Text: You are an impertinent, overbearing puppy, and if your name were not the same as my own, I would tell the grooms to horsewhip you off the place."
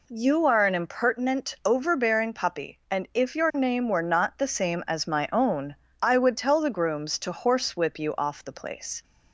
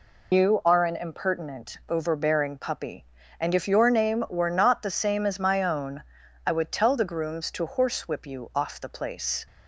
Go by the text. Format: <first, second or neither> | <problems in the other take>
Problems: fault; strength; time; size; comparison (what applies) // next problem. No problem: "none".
first | loses the start of "You"; at 0.3 s; 90 ms